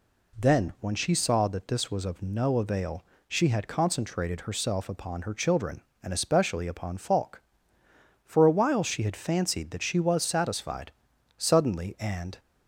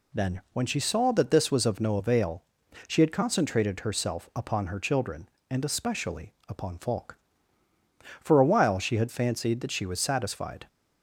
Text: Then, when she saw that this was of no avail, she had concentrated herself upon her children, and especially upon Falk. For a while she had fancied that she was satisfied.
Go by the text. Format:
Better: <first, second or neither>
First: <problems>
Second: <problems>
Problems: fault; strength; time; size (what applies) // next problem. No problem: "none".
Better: second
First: goes on to say "Suddenly and"; noticeable; from 11.3 s on; 1.0 s long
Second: none